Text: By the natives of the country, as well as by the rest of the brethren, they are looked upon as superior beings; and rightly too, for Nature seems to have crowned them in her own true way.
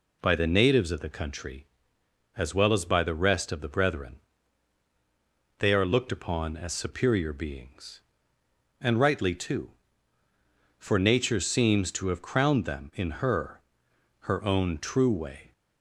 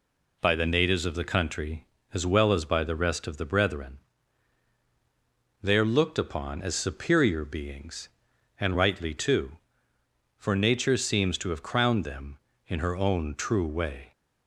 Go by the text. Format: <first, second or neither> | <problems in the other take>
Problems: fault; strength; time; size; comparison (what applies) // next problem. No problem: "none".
second | says "her" twice; at 14.2 s